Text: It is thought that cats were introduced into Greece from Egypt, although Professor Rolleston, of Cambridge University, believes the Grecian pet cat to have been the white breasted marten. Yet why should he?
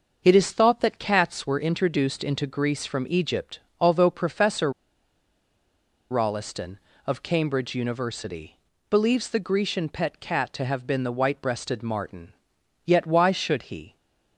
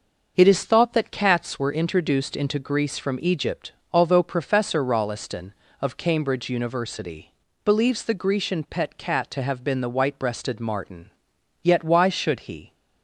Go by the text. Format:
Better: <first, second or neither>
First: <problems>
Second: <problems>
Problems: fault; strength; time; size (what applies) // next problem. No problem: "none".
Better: second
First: starts louder than the rest; noticeable; until 1.2 s; 6 dB // pauses between "Professor" and "Rolleston"; strong; at 4.7 s; 1.4 s long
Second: starts louder than the rest; noticeable; until 1.3 s; 6 dB